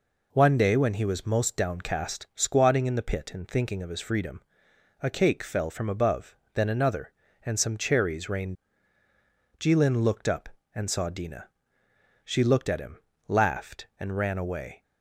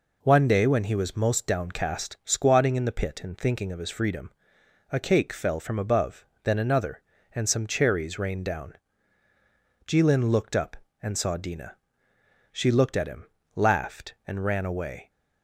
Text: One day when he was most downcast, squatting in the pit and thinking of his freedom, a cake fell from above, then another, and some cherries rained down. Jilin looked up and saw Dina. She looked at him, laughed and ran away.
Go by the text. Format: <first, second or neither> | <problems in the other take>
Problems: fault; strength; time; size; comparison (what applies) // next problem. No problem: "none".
second | skips "down"; at 9.0 s